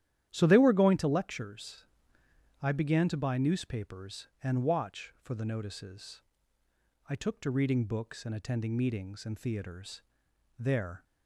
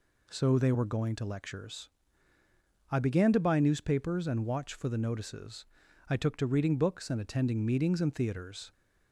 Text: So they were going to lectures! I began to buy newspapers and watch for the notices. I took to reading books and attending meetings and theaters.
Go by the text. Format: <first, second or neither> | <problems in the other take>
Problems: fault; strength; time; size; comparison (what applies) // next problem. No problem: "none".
second | starts louder than the rest; strong; until 1.3 s; 11 dB // goes on to say "There"; slight; from 10.5 s on; 0.44 s long